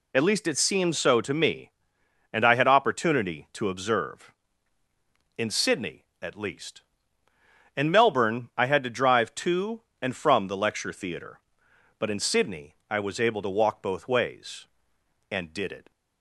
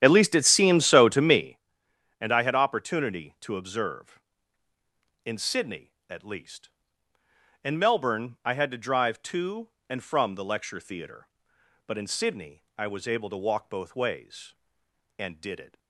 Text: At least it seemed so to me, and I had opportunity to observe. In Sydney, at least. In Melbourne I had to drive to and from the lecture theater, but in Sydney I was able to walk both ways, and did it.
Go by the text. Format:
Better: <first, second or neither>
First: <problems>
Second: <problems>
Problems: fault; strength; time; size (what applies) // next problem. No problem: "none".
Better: first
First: none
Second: starts louder than the rest; strong; until 1.6 s; 10 dB